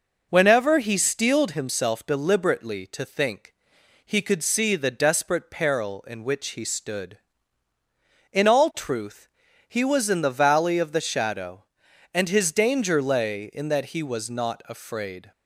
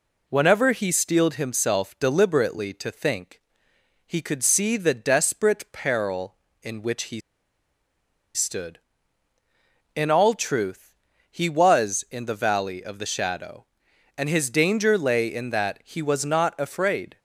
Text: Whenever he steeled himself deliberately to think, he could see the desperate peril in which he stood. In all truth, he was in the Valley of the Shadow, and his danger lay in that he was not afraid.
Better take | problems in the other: first | pauses between "he" and "stood"; at 7.1 s; 1.1 s long

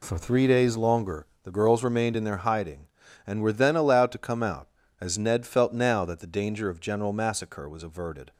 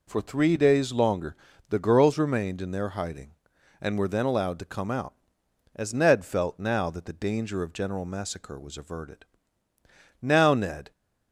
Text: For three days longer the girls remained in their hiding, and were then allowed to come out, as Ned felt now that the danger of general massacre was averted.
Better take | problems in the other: first | pauses between "longer" and "the"; slight; at 1.3 s; 0.32 s long; slight in the first // goes on to say "Now Ned"; noticeable; from 10.2 s on; 0.70 s long

